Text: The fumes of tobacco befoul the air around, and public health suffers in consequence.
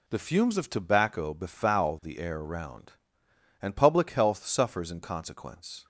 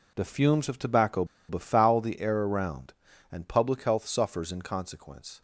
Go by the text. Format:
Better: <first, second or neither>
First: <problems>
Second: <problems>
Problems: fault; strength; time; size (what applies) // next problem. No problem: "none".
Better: first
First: none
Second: pauses between "tobacco" and "befoul"; slight; at 1.2 s; 0.23 s long